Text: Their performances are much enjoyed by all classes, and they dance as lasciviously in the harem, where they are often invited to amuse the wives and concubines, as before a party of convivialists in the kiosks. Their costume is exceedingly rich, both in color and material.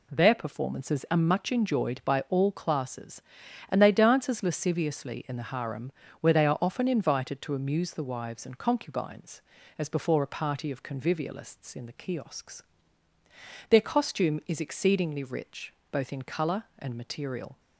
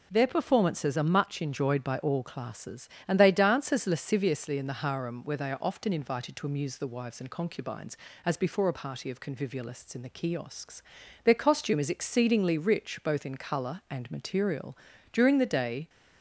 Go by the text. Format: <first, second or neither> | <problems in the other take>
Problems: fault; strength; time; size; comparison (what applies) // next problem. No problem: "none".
first | goes on to say "During the day"; noticeable; from 15.1 s on; 0.76 s long